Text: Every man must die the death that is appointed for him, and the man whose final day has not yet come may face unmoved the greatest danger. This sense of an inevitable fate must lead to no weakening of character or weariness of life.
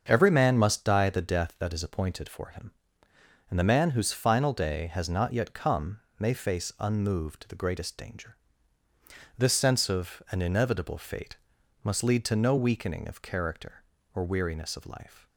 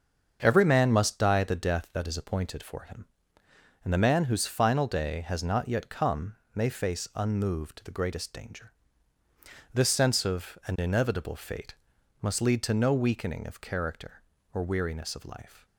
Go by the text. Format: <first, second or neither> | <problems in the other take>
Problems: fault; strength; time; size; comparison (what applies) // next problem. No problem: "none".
neither | starts louder than the rest; the same in both // pauses between "come" and "may"; slight; the same in both // pauses between "fate" and "must"; noticeable; the same in both